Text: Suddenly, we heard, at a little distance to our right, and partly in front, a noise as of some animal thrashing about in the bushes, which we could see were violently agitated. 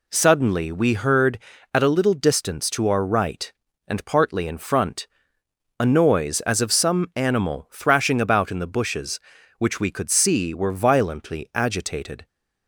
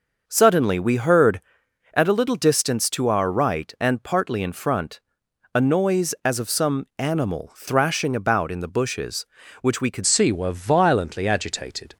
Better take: first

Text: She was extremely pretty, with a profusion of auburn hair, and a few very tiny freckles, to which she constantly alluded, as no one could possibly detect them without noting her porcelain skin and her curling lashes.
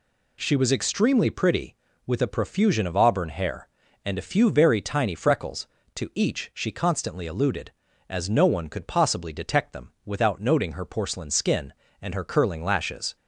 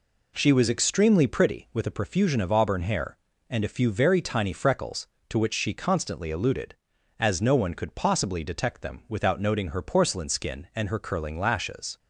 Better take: second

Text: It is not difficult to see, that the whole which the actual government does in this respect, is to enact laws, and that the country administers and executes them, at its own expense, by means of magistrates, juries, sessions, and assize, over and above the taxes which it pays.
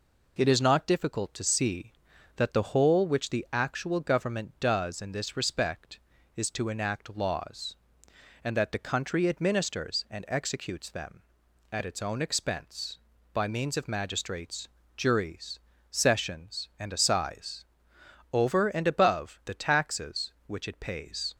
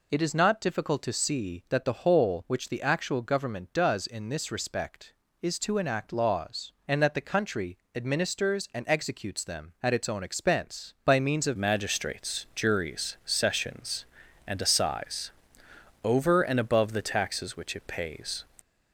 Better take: first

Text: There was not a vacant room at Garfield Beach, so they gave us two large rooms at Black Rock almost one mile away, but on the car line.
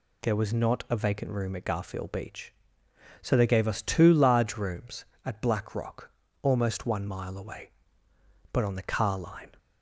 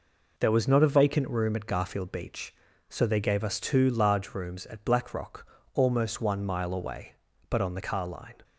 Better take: neither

